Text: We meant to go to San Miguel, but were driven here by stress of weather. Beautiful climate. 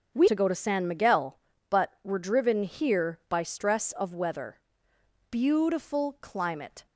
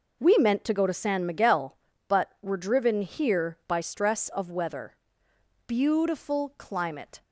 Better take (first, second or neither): second